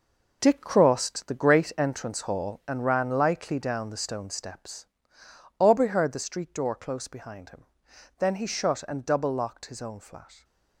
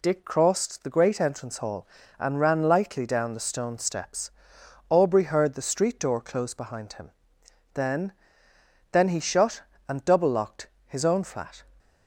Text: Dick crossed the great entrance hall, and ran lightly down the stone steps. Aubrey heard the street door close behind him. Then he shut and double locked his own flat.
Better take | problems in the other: first | says "Then" twice; at 8.9 s // pauses between "locked" and "his"; slight; at 10.6 s; 0.18 s long

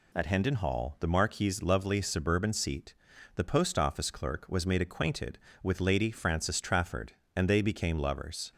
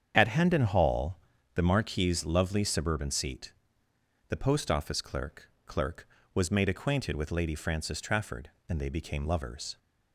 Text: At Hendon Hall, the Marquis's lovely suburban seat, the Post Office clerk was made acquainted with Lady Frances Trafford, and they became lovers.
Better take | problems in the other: first | starts louder than the rest; strong; until 1.1 s; 8 dB // says "clerk" twice; at 5.6 s

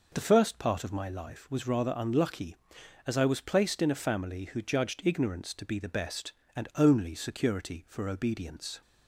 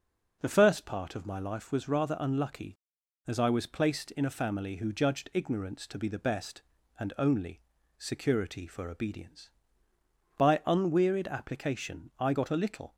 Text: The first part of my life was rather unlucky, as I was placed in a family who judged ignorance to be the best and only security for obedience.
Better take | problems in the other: first | pauses between "only" and "security"; at 7.6 s; 0.38 s long // goes on to say "By unwearied application I got a little"; strong; from 10.3 s on; 2.5 s long

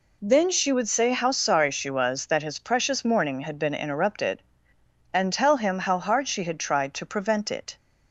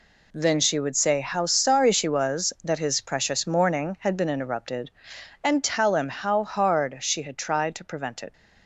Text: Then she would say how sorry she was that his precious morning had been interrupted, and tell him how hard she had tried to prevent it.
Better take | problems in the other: neither | none

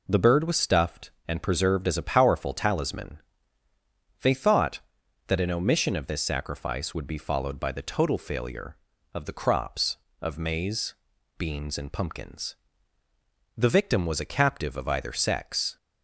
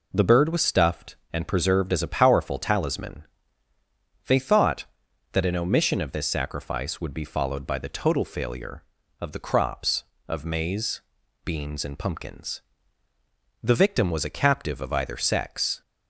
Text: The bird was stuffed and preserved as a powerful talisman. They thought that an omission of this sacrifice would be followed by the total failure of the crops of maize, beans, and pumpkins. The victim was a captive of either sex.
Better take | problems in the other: neither | none

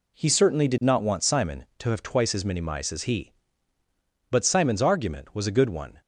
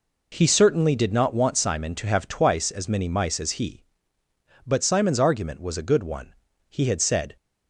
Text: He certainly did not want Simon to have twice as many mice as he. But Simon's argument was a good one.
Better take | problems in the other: first | goes on to say "He had said"; noticeable; from 6.6 s on; 0.66 s long

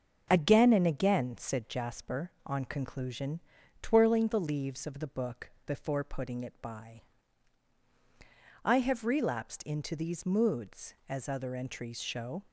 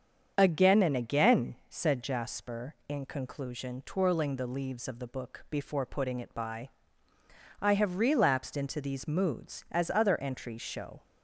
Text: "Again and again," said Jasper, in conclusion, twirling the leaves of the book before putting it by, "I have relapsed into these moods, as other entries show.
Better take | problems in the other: second | starts louder than the rest; noticeable; until 1.3 s; 6 dB; strong in the second // says "on" for "in"; at 2.4 s // pauses between "book" and "before"; slight; at 5.4 s; 0.16 s long

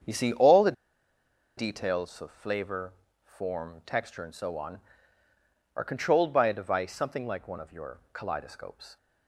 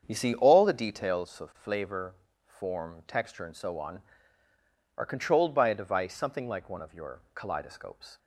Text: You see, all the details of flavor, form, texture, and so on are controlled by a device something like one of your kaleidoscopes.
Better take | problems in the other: second | starts louder than the rest; strong; until 1.9 s; 7.5 dB; strong in the second // pauses between "the" and "details"; noticeable; at 0.7 s; 0.85 s long

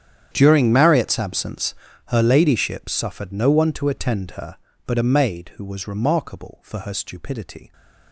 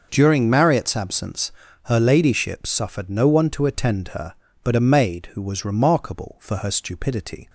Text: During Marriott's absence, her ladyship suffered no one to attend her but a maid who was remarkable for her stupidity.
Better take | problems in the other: second | gets quieter; strong; throughout; 19.5 dB

